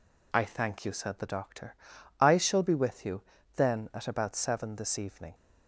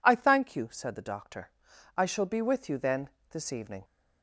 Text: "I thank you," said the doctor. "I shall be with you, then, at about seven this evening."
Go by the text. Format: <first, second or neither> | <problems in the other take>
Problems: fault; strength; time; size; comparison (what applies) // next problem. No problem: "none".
first | skips "at about seven"; at 3.2 s